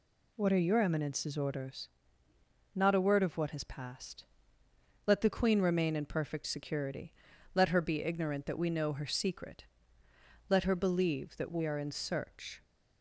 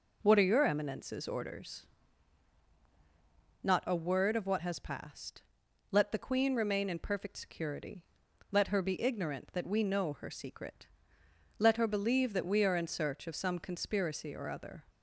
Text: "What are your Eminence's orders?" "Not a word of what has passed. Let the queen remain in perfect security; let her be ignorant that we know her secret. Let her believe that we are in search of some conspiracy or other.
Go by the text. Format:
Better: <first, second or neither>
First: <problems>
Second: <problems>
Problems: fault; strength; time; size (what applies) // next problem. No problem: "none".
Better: second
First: stops before "of some conspiracy or other"; at 12.6 s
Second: none